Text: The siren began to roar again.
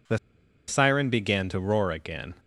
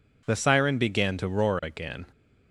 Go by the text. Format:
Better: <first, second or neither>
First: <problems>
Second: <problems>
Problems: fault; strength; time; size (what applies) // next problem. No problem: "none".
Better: second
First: pauses between "The" and "siren"; noticeable; at 0.1 s; 0.49 s long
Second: none